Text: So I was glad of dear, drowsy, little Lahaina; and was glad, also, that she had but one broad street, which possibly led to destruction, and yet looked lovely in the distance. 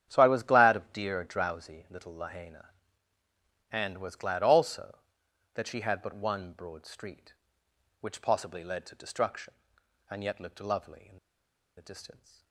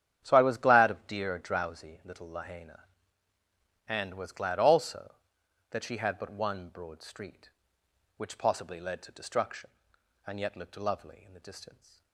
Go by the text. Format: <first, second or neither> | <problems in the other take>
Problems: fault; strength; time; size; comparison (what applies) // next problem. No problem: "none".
second | starts louder than the rest; strong; until 1.1 s; 9.5 dB; strong in the second // pauses between "in" and "the"; noticeable; at 11.1 s; 0.58 s long